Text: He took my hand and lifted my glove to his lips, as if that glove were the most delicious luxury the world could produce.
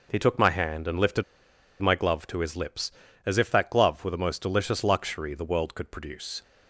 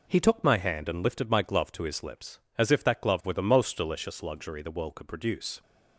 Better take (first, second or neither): second